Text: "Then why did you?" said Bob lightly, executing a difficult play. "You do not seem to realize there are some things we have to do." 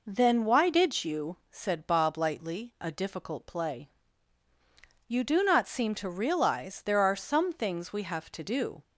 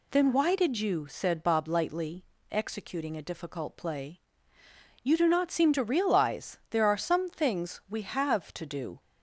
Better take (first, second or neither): second